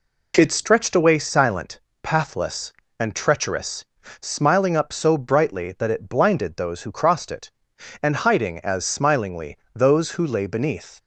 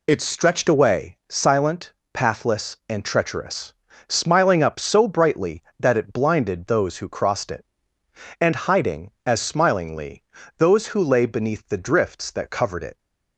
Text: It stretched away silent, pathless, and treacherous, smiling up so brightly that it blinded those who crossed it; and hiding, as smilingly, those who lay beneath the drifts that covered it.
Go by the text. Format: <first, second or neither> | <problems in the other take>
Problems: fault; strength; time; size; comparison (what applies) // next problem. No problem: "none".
second | stops before "the drifts that covered it"; at 10.9 s